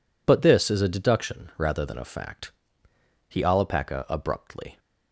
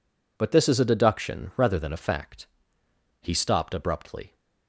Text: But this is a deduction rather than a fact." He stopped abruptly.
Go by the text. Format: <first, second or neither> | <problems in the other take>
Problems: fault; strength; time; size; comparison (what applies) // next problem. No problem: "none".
second | says "alapaca" for "stopped"; at 3.4 s